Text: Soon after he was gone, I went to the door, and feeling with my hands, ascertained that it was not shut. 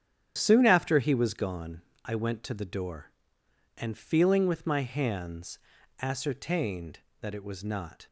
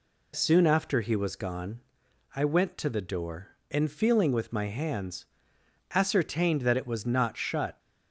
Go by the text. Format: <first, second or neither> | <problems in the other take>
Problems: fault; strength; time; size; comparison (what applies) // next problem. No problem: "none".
second | starts louder than the rest; strong; until 1.3 s; 9 dB // stops before "shut"; at 8.0 s